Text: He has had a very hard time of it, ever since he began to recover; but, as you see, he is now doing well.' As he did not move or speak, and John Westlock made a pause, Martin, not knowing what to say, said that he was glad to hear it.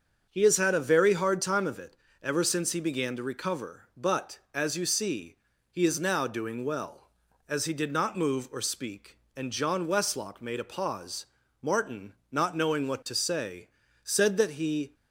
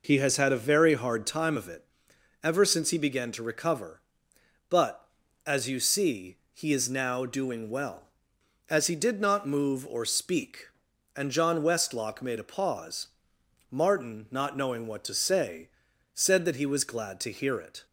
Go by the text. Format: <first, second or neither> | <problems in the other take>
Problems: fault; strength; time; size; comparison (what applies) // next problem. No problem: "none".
second | starts louder than the rest; until 1.2 s; 7 dB // stops before "was glad to hear it"; at 14.9 s